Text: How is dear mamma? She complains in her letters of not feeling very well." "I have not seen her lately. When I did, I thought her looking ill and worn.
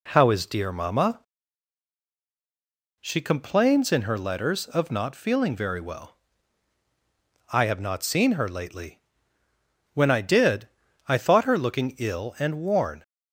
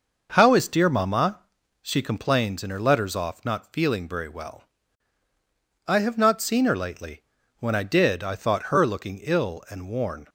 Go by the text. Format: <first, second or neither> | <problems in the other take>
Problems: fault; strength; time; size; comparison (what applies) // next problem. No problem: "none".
first | says "off" for "of"; at 3.1 s